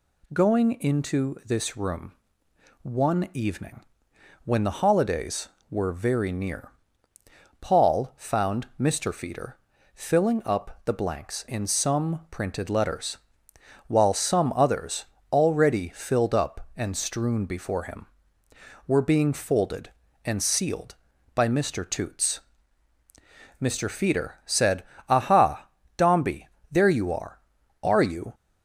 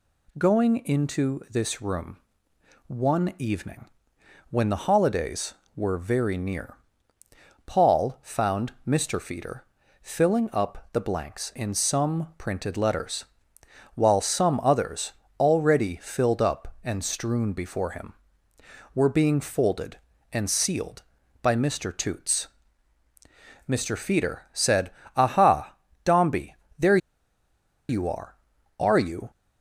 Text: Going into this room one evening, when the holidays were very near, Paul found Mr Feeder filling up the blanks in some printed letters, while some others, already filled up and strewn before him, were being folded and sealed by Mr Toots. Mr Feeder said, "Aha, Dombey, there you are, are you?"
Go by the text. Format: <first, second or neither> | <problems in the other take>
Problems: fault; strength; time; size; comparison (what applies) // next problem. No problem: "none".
first | pauses between "room" and "one"; noticeable; at 2.1 s; 0.68 s long; noticeable in the first // pauses between "Feeder" and "filling"; at 9.6 s; 0.40 s long; also in the first // pauses between "there" and "you"; noticeable; at 26.9 s; 0.91 s long